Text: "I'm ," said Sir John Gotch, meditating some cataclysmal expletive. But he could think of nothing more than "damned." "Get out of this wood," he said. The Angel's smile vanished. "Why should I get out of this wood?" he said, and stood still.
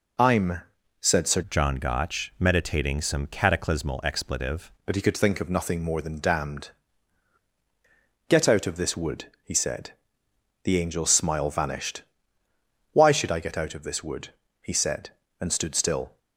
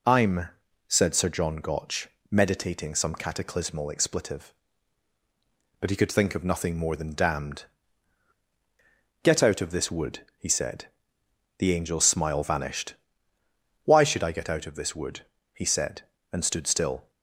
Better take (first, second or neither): second